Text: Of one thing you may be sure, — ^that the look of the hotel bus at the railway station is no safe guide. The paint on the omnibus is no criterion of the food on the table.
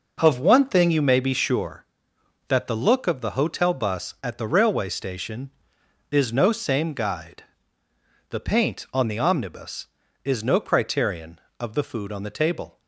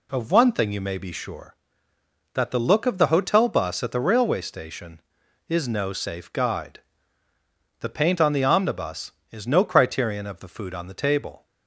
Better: second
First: says "same" for "safe"; at 6.5 s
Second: none

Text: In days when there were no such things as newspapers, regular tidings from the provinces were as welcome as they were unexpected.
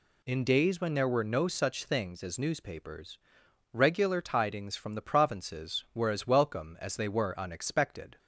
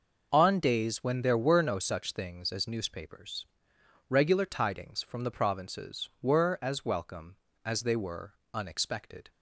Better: first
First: none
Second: says "On" for "In"; at 0.3 s // pauses between "were" and "unexpected"; slight; at 8.3 s; 0.18 s long

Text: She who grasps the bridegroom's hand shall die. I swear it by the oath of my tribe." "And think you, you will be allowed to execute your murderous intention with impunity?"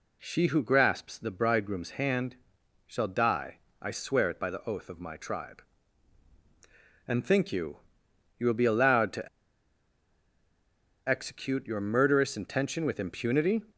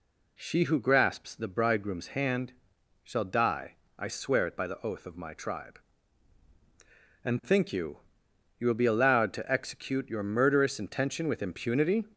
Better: second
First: pauses between "hand" and "shall"; noticeable; at 2.3 s; 0.50 s long // pauses between "to" and "execute"; strong; at 9.2 s; 1.8 s long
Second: pauses between "hand" and "shall"; noticeable; at 2.5 s; 0.50 s long

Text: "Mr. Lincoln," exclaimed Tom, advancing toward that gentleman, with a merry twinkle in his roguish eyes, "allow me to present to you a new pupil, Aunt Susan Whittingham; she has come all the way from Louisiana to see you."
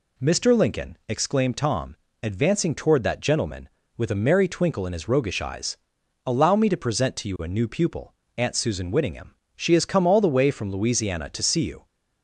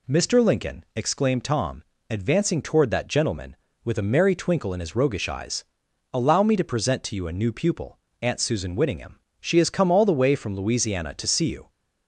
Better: neither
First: none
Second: none

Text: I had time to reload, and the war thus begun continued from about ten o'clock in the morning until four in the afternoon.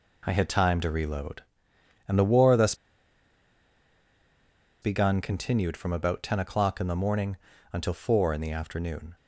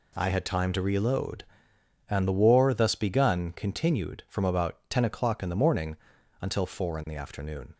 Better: second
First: pauses between "thus" and "begun"; strong; at 2.7 s; 2.0 s long // pauses between "morning" and "until"; slight; at 7.3 s; 0.36 s long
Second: pauses between "morning" and "until"; at 5.9 s; 0.44 s long

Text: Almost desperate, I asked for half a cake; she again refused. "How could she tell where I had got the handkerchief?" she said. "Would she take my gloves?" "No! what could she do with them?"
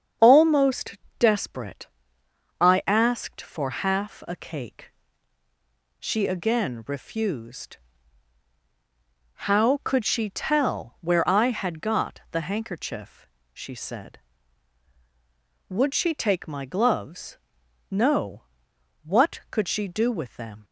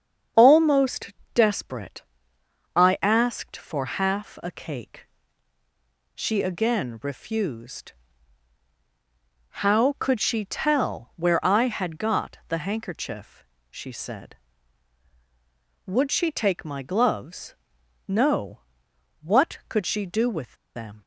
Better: first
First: starts louder than the rest; strong; until 1.4 s; 7.5 dB // pauses between "Almost" and "desperate"; slight; at 0.9 s; 0.20 s long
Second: starts louder than the rest; strong; until 1.5 s; 7.5 dB // pauses between "Almost" and "desperate"; slight; at 1.1 s; 0.20 s long // pauses between "with" and "them"; slight; at 20.5 s; 0.21 s long

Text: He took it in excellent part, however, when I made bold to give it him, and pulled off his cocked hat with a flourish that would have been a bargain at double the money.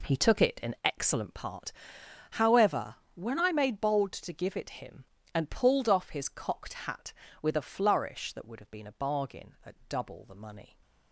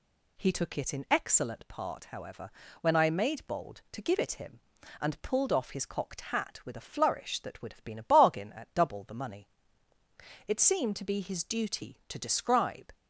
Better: first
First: none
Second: goes on to say "It seemed to be his duty to describe"; strong; from 10.4 s on; 2.4 s long

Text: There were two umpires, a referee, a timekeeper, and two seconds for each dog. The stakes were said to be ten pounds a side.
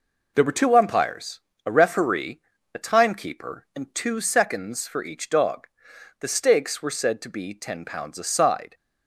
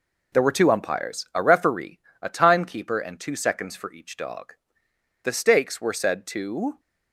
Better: first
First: none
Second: stops before "be ten pounds a side"; at 6.7 s

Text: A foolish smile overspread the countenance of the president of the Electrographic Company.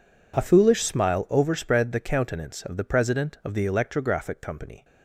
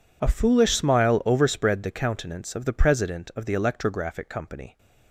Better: neither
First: none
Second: none

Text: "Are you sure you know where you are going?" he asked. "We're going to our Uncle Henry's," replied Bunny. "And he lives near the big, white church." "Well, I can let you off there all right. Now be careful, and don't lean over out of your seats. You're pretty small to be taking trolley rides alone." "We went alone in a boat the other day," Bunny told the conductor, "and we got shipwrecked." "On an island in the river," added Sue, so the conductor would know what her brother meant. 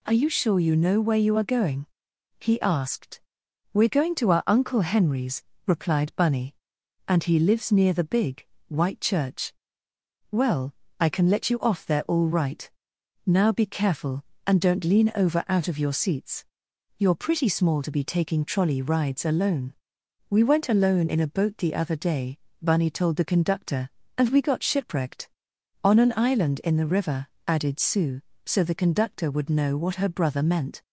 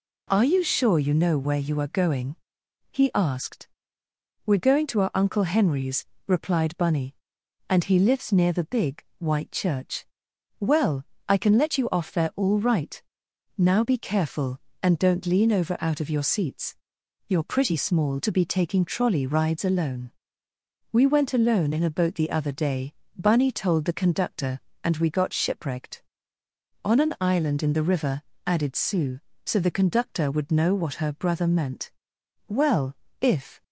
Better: first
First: none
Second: goes on to say "Well if"; noticeable; from 32.4 s on; 1.1 s long

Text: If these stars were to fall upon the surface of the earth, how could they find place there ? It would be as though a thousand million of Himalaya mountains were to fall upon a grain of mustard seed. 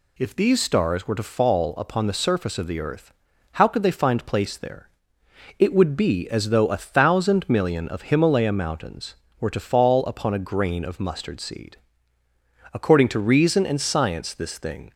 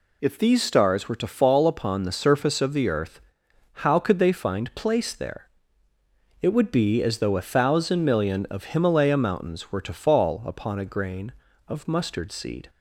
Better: second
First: goes on to say "According to reason and science this thing"; strong; from 12.7 s on; 2.2 s long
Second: none

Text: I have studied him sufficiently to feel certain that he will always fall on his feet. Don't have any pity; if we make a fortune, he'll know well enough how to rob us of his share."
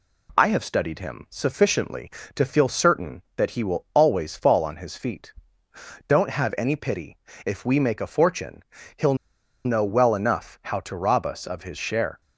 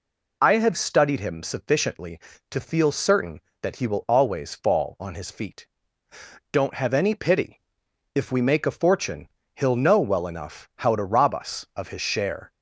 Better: second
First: pauses between "he'll" and "know"; noticeable; at 9.1 s; 0.50 s long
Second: none

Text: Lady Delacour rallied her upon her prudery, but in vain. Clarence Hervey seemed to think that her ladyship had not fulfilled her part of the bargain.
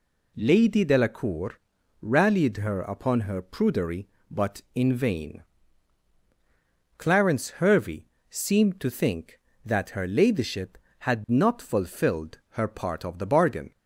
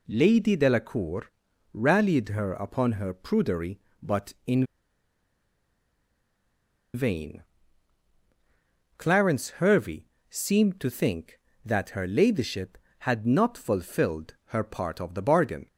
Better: first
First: pauses between "Delacour" and "rallied"; at 1.5 s; 0.42 s long // pauses between "Hervey" and "seemed"; slight; at 8.0 s; 0.24 s long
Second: pauses between "Delacour" and "rallied"; at 1.3 s; 0.42 s long // pauses between "in" and "vain"; strong; at 4.6 s; 2.3 s long // pauses between "Hervey" and "seemed"; slight; at 10.0 s; 0.24 s long

